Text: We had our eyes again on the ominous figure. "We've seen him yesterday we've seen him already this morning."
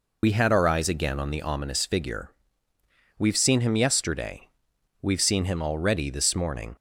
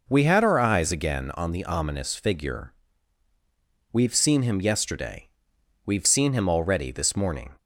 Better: second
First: loses the start of "We"; at 0.2 s; 65 ms // pauses between "yesterday" and "we've"; noticeable; at 4.4 s; 0.52 s long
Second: pauses between "yesterday" and "we've"; noticeable; at 5.2 s; 0.58 s long

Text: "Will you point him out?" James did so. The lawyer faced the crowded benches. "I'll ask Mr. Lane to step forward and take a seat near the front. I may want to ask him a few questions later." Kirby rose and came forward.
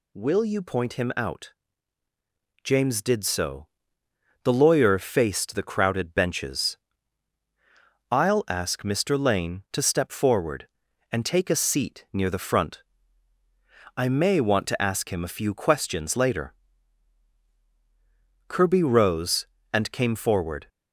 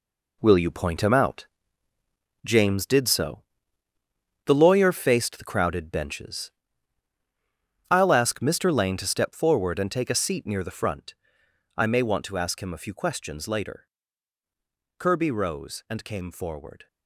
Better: first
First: none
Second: gets quieter; strong; throughout; 9 dB

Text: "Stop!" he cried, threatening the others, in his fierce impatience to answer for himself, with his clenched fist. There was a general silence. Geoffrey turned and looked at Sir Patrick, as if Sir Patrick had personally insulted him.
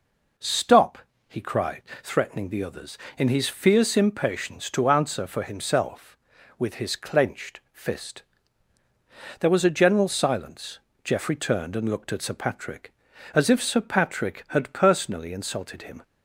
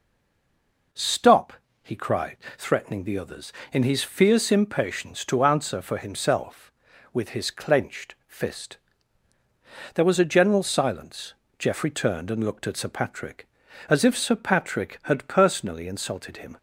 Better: first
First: none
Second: stays silent before the first word; slight; until 0.9 s; 0.9 s long

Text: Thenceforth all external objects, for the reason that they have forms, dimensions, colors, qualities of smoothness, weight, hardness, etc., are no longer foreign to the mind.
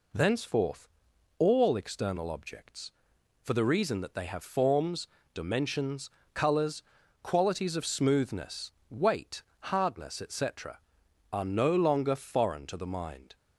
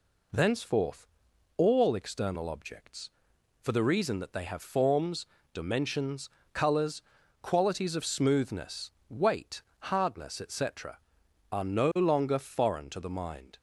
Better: neither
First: pauses between "Thenceforth" and "all"; noticeable; at 0.8 s; 0.50 s long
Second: pauses between "Thenceforth" and "all"; noticeable; at 1.0 s; 0.50 s long

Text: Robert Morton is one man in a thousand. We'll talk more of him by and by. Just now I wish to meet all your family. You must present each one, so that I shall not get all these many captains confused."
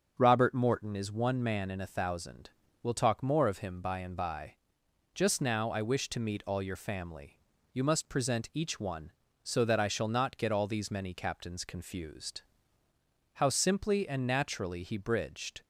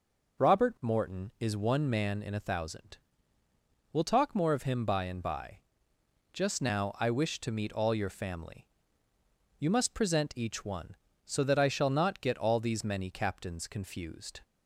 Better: second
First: starts louder than the rest; until 1.1 s; 6.5 dB // goes on to say "How simply and naturally he bridged"; strong; from 13.3 s on; 2.2 s long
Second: none

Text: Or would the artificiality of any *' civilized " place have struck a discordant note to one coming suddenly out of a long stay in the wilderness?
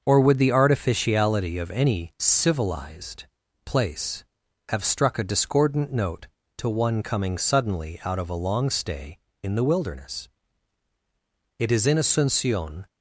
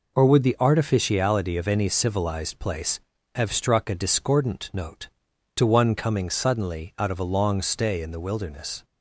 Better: second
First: starts louder than the rest; until 1.0 s; 6.5 dB // goes on to say "It is in Asuncion"; noticeable; from 11.5 s on; 1.2 s long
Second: none

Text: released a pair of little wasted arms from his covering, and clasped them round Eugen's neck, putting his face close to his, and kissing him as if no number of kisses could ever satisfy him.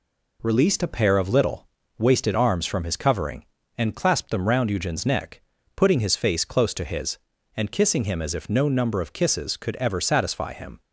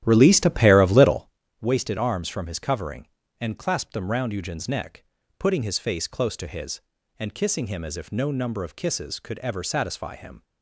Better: first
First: pauses between "little" and "wasted"; slight; at 1.6 s; 0.30 s long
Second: starts louder than the rest; strong; until 1.3 s; 12 dB // pauses between "little" and "wasted"; slight; at 1.2 s; 0.30 s long

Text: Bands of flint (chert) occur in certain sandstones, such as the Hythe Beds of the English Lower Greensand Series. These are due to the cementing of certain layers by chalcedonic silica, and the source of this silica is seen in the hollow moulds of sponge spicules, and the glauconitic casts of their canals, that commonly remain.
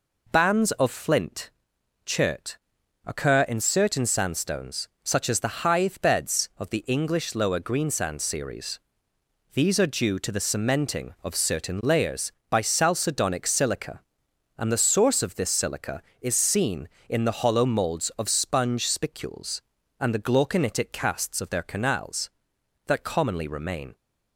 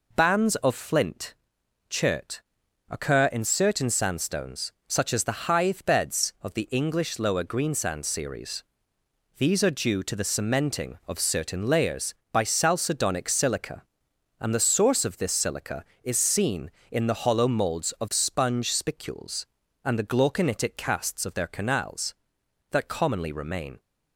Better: neither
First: none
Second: none

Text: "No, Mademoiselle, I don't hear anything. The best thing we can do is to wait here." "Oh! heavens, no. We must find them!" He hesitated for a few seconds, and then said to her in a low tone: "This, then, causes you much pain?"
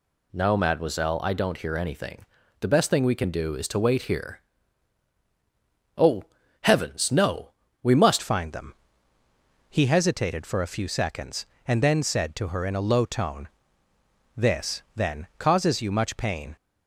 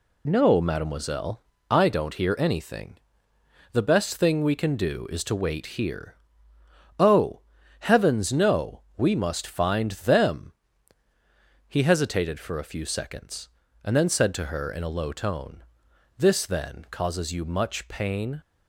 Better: second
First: changes voice at "find"; from 8.2 s on; 8.3 s long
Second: none

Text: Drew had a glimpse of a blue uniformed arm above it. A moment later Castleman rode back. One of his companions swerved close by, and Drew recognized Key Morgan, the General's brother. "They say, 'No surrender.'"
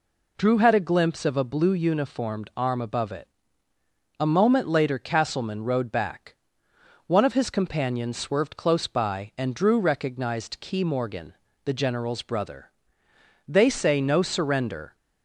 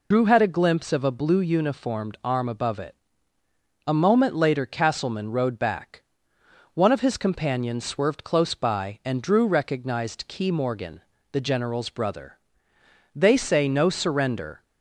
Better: first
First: none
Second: loses the start of "Drew"; at 0.1 s; 60 ms

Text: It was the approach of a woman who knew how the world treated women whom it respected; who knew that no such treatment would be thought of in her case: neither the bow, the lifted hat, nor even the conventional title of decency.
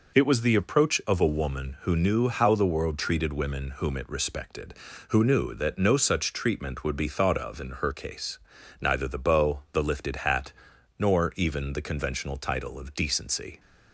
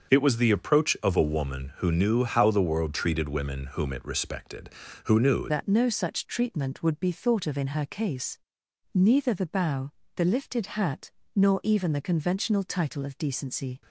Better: first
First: none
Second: starts louder than the rest; until 1.1 s; 6.5 dB // changes voice at "that"; from 5.4 s on; 8.4 s long

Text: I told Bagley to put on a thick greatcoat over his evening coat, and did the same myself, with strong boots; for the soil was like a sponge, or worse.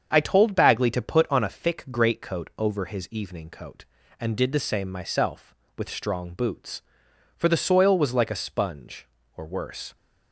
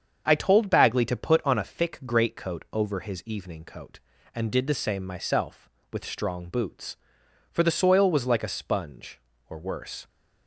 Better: neither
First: starts louder than the rest; until 1.1 s; 7 dB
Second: starts louder than the rest; until 1.2 s; 7 dB

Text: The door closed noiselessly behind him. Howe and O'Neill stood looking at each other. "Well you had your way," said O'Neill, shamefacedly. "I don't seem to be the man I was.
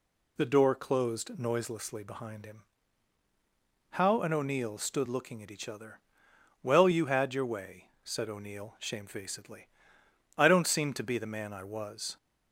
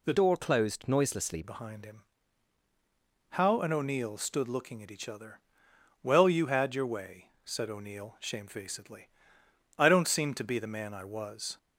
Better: first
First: none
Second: changes voice from "door" to "noiselessly"; from 0.1 to 1.4 s; 1.3 s long

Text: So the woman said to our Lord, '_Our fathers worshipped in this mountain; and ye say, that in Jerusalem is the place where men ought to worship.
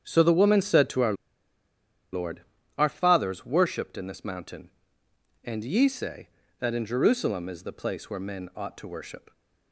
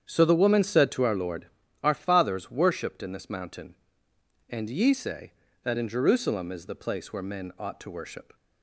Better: second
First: starts louder than the rest; strong; until 1.1 s; 8.5 dB // pauses between "our" and "Lord"; at 1.1 s; 0.99 s long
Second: starts louder than the rest; strong; until 1.1 s; 8.5 dB

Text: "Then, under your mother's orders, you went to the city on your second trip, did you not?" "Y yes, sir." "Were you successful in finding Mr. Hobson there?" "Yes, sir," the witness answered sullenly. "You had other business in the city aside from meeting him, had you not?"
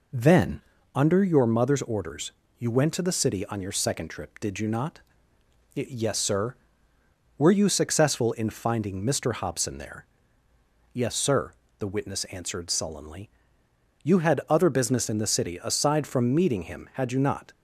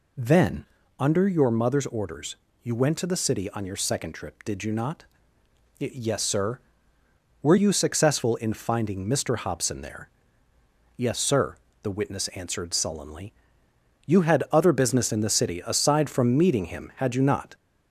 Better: first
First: none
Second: gets louder; slight; throughout; 2.5 dB

